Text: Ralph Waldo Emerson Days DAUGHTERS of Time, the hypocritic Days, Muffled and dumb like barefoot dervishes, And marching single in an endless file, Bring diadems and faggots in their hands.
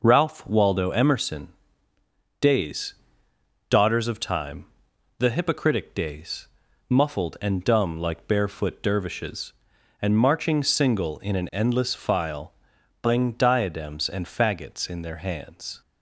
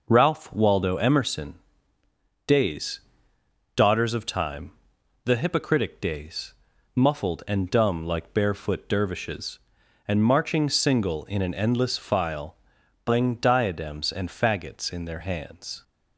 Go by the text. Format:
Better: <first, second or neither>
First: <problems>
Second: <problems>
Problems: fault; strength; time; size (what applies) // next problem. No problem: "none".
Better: neither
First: pauses between "Emerson" and "Days"; noticeable; at 1.4 s; 0.90 s long // pauses between "Days" and "DAUGHTERS"; noticeable; at 2.9 s; 0.74 s long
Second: pauses between "Emerson" and "Days"; noticeable; at 1.5 s; 0.90 s long // pauses between "Days" and "DAUGHTERS"; noticeable; at 3.0 s; 0.74 s long